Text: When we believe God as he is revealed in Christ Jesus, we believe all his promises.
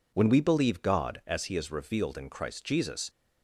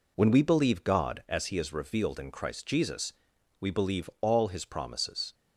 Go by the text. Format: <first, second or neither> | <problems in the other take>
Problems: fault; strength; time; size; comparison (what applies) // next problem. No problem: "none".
second | stops before "we believe all his promises"; at 3.0 s